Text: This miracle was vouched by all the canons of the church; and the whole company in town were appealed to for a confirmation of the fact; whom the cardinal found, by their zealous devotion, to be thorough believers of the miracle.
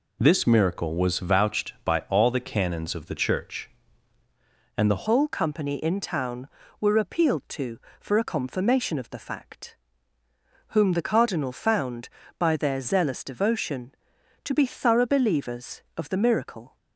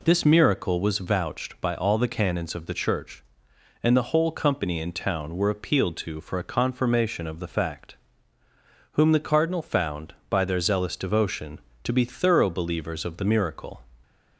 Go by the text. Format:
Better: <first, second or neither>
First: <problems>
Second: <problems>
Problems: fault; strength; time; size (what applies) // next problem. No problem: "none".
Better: second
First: changes voice at "whole"; from 5.0 s on; 11.7 s long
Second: none